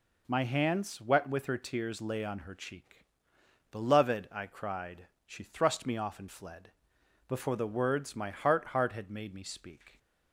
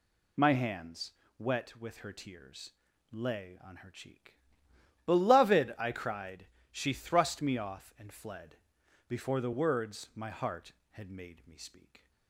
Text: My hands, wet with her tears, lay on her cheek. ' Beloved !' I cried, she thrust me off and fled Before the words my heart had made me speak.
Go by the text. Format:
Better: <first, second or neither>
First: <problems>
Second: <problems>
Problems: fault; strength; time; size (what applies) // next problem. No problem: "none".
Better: second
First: pauses between "fled" and "Before"; noticeable; at 6.6 s; 0.56 s long // says "heart" twice; at 8.6 s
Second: pauses between "fled" and "Before"; noticeable; at 8.5 s; 0.52 s long